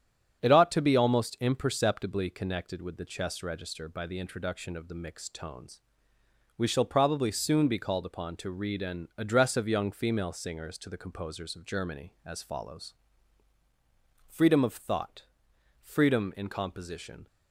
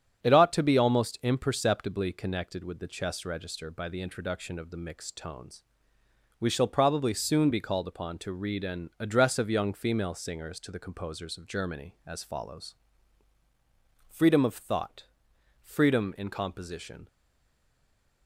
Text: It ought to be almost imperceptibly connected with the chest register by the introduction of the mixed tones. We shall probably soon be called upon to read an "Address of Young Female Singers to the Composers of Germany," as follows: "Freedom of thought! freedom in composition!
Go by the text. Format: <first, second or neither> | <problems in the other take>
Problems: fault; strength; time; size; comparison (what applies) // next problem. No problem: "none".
first | starts louder than the rest; strong; until 1.2 s; 9 dB; strong in the first // stays silent after the last word; noticeable; from 17.0 s on; 1.2 s long